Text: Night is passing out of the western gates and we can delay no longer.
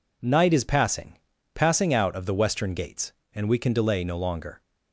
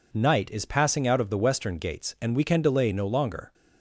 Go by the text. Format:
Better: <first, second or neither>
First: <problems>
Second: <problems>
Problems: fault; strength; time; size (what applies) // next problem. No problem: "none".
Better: second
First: says "passing" twice; at 1.5 s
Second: none